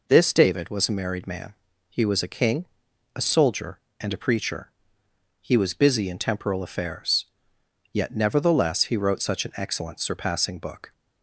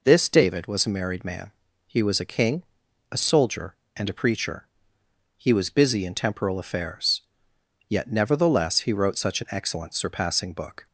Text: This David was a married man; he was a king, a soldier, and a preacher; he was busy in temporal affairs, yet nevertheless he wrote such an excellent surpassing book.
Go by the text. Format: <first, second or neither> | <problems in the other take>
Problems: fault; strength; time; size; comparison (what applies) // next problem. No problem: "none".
neither | none